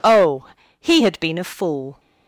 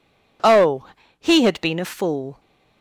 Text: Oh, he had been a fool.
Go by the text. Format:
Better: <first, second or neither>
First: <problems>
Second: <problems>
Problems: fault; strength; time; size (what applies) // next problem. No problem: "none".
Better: neither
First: none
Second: none